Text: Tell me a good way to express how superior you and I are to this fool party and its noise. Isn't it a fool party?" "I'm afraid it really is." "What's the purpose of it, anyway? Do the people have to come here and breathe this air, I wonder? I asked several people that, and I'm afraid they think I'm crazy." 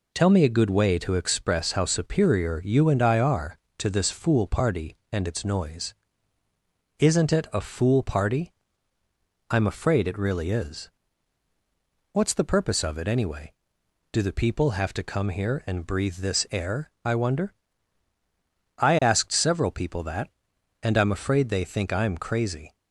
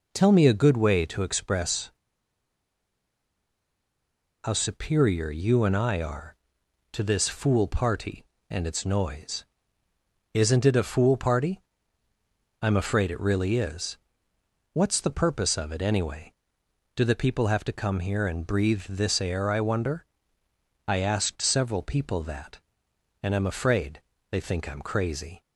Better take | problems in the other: first | pauses between "express" and "how"; strong; at 1.9 s; 2.5 s long // pauses between "afraid" and "they"; slight; at 24.0 s; 0.28 s long

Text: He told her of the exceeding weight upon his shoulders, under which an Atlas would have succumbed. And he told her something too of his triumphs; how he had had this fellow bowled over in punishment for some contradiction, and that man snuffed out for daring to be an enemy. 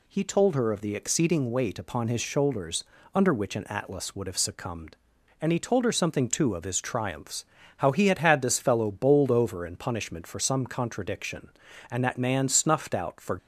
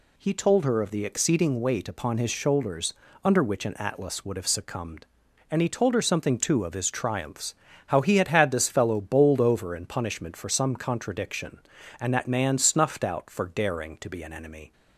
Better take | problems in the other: second | stops before "daring to be an enemy"; at 13.3 s

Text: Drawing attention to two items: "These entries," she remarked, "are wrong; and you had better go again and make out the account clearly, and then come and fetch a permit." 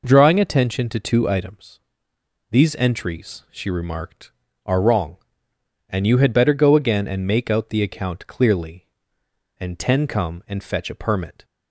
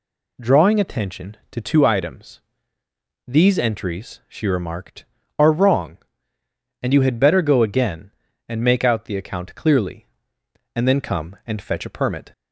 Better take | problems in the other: second | says "ten" for "then"; at 9.7 s

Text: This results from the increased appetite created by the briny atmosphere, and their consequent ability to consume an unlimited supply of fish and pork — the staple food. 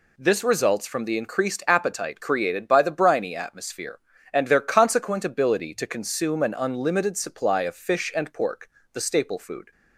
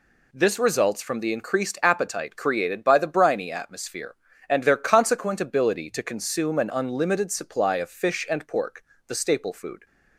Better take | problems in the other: neither | none

